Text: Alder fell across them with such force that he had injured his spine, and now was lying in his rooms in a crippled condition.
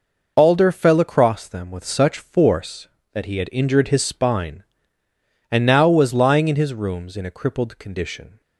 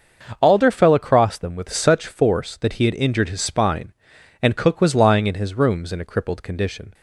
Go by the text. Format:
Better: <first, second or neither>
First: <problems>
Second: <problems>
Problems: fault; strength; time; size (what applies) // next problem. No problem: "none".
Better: first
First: none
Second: starts louder than the rest; until 1.4 s; 6 dB // says "cook" for "now"; at 4.5 s